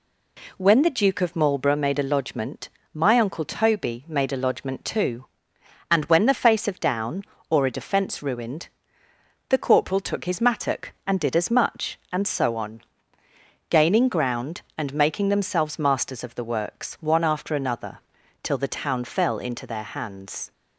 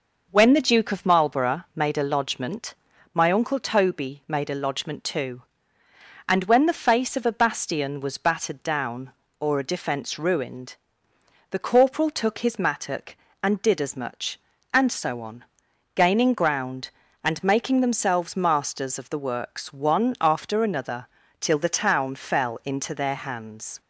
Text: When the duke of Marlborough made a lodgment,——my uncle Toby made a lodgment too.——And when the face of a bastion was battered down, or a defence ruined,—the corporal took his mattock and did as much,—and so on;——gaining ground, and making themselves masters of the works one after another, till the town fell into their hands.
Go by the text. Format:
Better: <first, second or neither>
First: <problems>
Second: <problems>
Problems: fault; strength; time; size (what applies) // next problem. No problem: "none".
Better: second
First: skips "a bastion was battered"; at 6.8 s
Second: none